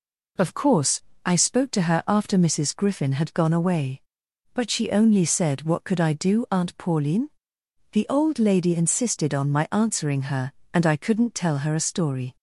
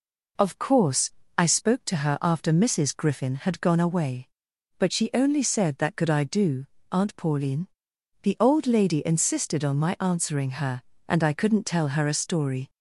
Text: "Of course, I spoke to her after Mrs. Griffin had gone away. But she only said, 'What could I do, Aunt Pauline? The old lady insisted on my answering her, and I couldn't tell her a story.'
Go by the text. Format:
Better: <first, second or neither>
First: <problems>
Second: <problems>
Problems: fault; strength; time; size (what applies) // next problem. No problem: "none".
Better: first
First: none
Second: says "That" for "What"; at 5.7 s